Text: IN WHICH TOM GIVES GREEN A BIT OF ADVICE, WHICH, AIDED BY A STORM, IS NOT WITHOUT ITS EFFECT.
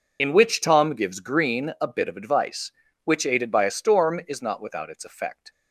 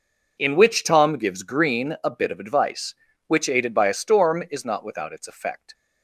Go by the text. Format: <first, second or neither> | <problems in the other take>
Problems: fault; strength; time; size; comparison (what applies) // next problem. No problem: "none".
second | loses the start of "IN"; at 0.1 s; 35 ms